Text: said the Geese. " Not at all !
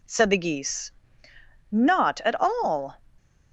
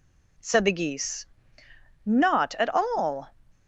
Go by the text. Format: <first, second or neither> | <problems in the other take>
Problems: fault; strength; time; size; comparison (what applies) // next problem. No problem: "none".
neither | none